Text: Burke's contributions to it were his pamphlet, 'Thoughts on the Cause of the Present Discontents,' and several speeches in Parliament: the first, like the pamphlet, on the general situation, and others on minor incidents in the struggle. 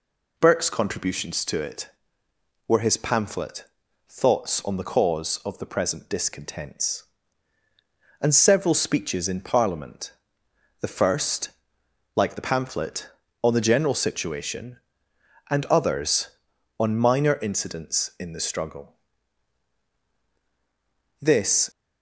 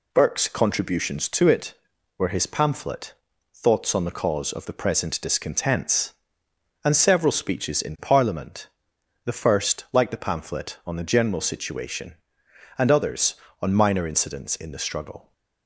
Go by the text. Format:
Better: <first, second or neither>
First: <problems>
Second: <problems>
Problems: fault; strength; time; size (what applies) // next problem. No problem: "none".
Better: second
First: goes on to say "This"; from 21.1 s on; 0.50 s long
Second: none